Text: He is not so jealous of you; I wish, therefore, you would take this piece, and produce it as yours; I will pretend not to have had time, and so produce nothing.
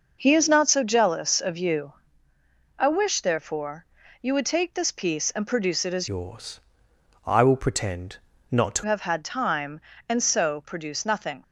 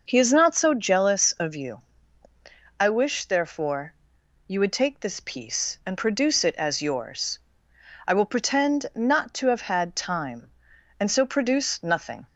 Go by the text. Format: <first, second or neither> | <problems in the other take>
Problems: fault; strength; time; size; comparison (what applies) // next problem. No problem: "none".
second | changes voice from "yours" to "to"; from 6.0 to 8.8 s; 2.8 s long // pauses between "pretend" and "not"; slight; at 8.1 s; 0.30 s long